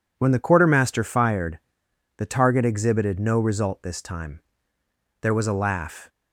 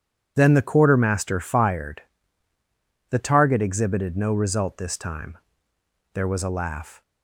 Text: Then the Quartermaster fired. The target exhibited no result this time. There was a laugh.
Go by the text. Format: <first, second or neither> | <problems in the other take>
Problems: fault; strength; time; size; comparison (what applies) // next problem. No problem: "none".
second | says "When" for "Then"; at 0.1 s